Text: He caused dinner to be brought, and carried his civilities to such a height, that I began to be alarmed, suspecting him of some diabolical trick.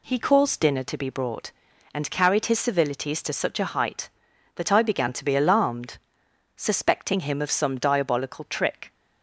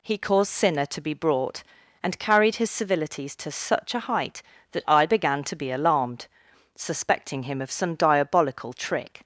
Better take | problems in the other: first | says "sinner" for "dinner"; at 0.5 s

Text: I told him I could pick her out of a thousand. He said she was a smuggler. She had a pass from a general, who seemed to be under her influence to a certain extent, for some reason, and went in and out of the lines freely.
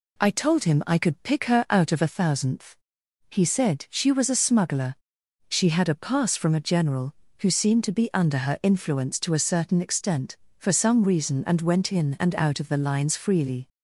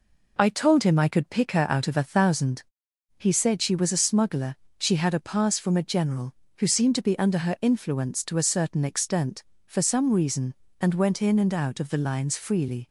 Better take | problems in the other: second | says "thousandth" for "thousand"; at 2.0 s

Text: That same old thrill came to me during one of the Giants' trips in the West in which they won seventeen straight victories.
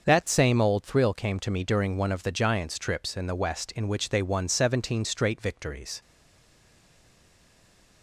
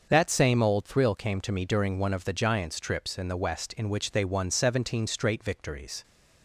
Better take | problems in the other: second | starts louder than the rest; until 1.1 s; 6.5 dB; also in the second // stays silent after the last word; noticeable; from 6.0 s on; 2.0 s long

